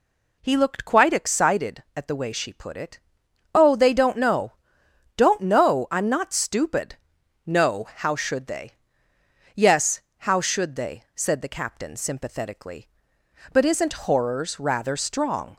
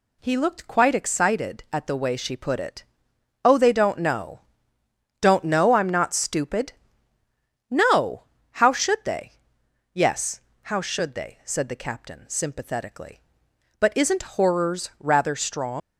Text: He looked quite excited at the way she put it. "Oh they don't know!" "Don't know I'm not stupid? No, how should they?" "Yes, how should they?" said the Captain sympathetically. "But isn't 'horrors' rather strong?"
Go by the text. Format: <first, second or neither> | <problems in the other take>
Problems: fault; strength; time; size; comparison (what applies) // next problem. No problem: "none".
first | leaves "strong" unfinished; at 15.8 s; 95 ms